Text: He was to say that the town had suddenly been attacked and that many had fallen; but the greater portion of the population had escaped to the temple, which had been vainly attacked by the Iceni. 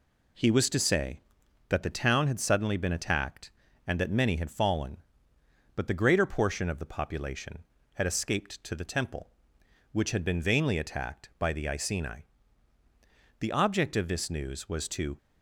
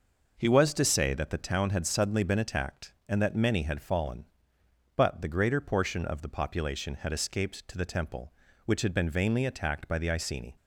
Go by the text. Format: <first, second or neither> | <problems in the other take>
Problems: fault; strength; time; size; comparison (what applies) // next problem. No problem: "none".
second | goes on to say "The object of this news was to"; strong; from 13.3 s on; 1.7 s long